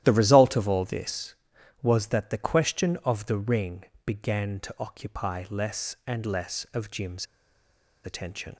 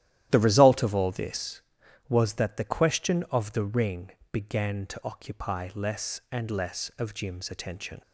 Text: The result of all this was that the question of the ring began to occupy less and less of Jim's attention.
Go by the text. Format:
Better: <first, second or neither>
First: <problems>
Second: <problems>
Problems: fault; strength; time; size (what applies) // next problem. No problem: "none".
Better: second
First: starts louder than the rest; strong; until 1.0 s; 12.5 dB // pauses between "ring" and "began"; slight; at 3.8 s; 0.20 s long // pauses between "Jim's" and "attention"; noticeable; at 7.2 s; 0.78 s long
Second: starts louder than the rest; strong; until 1.3 s; 12.5 dB // pauses between "ring" and "began"; slight; at 4.1 s; 0.20 s long